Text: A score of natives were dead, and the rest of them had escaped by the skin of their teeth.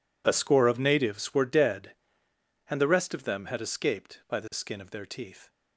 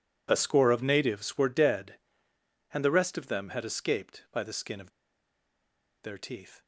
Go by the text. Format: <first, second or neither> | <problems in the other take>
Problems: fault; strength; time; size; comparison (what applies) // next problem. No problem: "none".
first | pauses between "of" and "their"; at 4.9 s; 1.1 s long